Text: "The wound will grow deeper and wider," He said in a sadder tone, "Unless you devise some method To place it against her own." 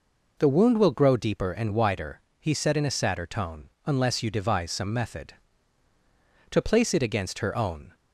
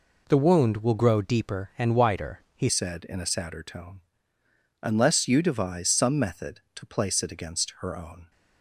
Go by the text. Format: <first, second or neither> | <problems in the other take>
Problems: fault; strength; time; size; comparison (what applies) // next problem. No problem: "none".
first | changes voice at "said"; from 2.6 s on; 5.7 s long